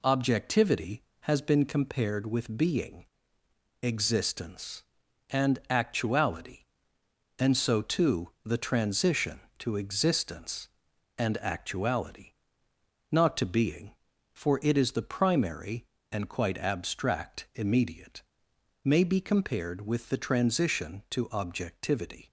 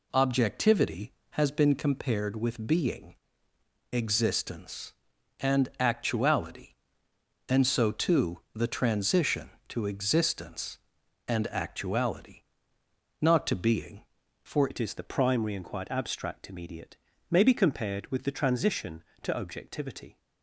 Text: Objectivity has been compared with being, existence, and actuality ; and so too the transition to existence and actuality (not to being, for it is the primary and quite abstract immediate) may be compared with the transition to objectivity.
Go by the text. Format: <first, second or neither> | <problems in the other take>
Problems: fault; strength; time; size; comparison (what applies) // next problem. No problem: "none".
first | changes voice at "it"; from 14.7 s on; 5.4 s long